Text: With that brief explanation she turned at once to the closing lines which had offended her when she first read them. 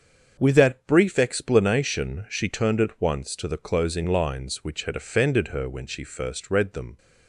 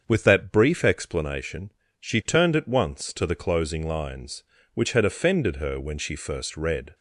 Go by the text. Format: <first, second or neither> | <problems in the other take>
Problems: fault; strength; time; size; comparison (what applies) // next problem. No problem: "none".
first | starts louder than the rest; until 1.0 s; 7 dB; also in the first // pauses between "explanation" and "she"; slight; at 1.7 s; 0.26 s long // stops before "them"; at 6.9 s